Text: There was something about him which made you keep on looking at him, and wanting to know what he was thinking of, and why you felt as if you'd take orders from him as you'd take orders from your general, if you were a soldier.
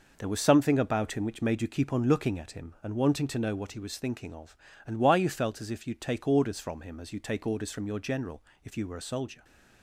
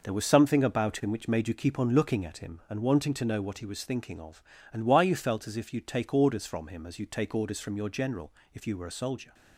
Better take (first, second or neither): neither